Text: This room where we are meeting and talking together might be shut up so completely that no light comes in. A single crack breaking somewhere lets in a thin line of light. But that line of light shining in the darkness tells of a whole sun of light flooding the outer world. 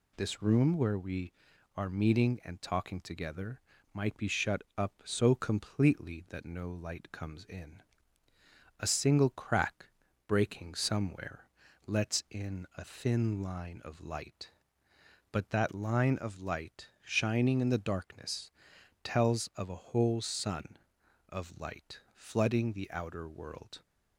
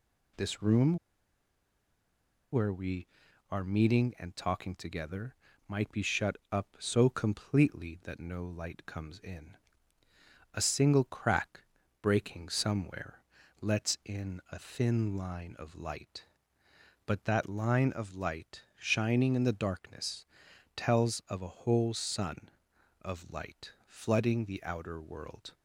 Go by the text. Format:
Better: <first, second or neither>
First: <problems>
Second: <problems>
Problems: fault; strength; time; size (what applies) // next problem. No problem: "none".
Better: first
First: pauses between "together" and "might"; slight; at 3.5 s; 0.36 s long // pauses between "shut" and "up"; slight; at 4.6 s; 0.16 s long // pauses between "crack" and "breaking"; at 9.8 s; 0.40 s long // pauses between "somewhere" and "lets"; at 11.4 s; 0.40 s long // pauses between "darkness" and "tells"; noticeable; at 18.5 s; 0.52 s long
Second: pauses between "room" and "where"; strong; at 0.9 s; 1.5 s long // pauses between "together" and "might"; slight; at 5.3 s; 0.36 s long // pauses between "shut" and "up"; slight; at 6.3 s; 0.16 s long // pauses between "crack" and "breaking"; at 11.6 s; 0.40 s long // pauses between "somewhere" and "lets"; at 13.2 s; 0.40 s long // pauses between "darkness" and "tells"; noticeable; at 20.2 s; 0.50 s long